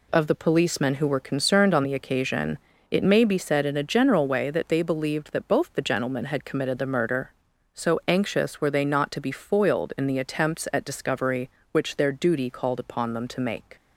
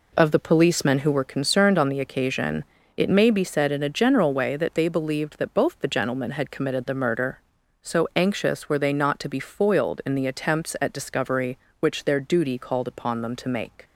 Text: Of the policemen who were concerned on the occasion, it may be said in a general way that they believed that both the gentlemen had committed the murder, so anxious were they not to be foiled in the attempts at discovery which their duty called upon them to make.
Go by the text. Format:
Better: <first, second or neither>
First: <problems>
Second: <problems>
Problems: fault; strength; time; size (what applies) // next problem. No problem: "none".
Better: first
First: none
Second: starts louder than the rest; until 1.2 s; 3.5 dB